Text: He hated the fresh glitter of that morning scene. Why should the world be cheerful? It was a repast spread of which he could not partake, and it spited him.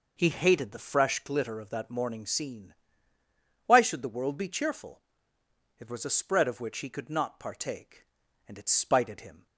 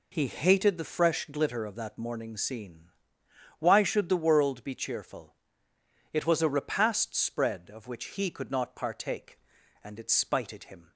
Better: second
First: skips "repast"; at 6.0 s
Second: none

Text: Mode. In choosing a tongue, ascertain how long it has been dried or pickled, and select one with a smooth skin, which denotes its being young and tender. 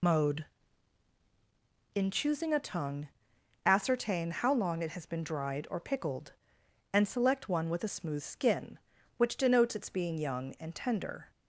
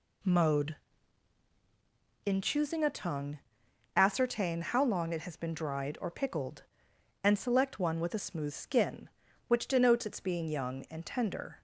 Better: second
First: loses the start of "Mode"; at 0.0 s; 100 ms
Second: none

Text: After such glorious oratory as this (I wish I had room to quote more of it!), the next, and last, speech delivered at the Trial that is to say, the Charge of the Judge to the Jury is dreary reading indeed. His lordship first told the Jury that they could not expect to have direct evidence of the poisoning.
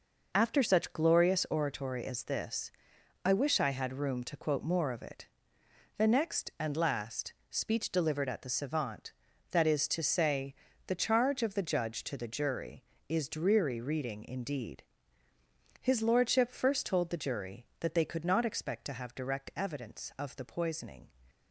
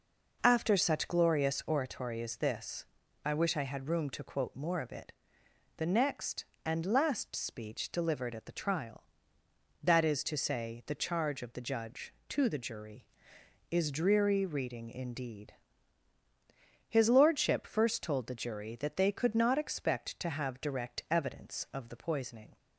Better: second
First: says "Savant" for "Trial"; at 8.4 s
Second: none

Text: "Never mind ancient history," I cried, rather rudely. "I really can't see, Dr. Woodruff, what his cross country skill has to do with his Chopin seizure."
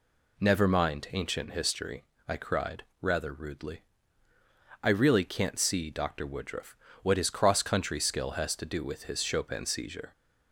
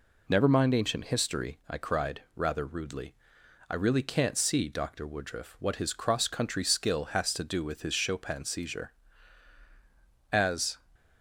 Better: first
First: none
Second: goes on to say "As"; slight; from 10.3 s on; 0.46 s long

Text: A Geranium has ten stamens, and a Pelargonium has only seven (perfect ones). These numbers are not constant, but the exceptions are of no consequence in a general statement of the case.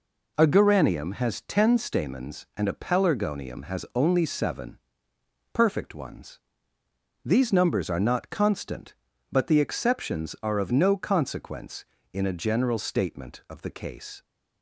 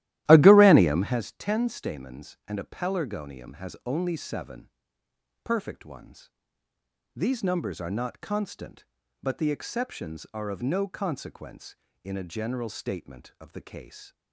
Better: first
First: none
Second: starts louder than the rest; strong; until 1.2 s; 14.5 dB

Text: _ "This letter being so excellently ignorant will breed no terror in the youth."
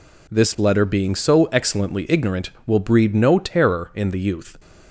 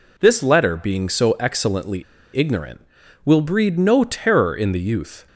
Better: first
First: none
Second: pauses between "excellently" and "ignorant"; slight; at 2.0 s; 0.32 s long

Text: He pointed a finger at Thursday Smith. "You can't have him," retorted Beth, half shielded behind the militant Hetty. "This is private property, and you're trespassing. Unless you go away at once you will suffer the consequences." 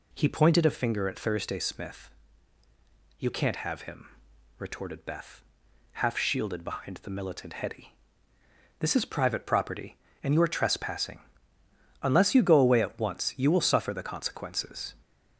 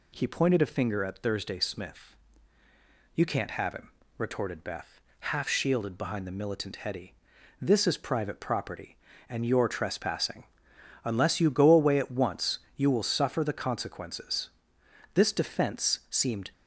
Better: first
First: none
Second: pauses between "once" and "you"; slight; at 12.5 s; 0.16 s long // goes on to say "This defense seemed"; from 15.1 s on; 1.3 s long

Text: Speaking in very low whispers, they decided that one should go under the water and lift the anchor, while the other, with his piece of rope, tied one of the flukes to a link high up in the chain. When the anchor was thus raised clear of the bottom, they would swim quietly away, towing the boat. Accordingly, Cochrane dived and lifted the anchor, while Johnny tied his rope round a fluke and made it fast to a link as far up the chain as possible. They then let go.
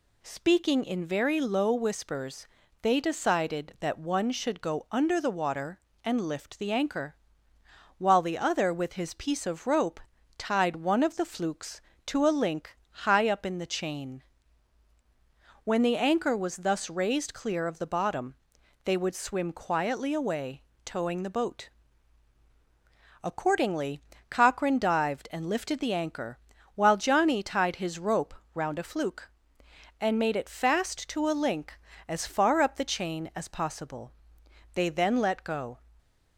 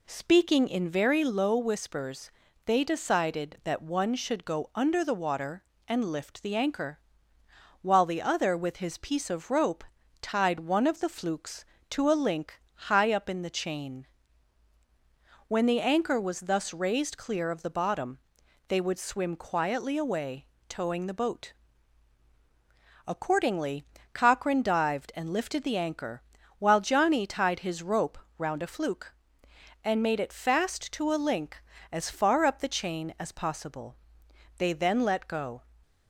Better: first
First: pauses between "link" and "high"; slight; at 12.7 s; 0.16 s long // pauses between "rope" and "round"; slight; at 28.3 s; 0.22 s long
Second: starts louder than the rest; slight; until 1.3 s; 2.5 dB // pauses between "link" and "high"; slight; at 12.5 s; 0.16 s long // pauses between "rope" and "round"; slight; at 28.1 s; 0.22 s long

